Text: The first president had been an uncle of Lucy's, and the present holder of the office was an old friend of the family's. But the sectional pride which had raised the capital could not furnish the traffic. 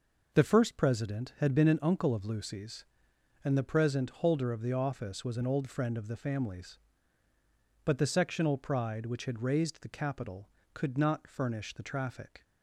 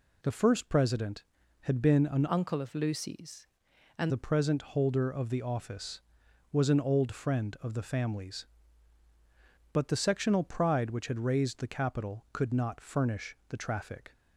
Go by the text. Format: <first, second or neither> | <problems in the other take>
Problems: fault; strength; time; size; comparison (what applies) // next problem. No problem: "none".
first | changes voice from "uncle" to "and"; from 2.2 to 4.1 s; 1.9 s long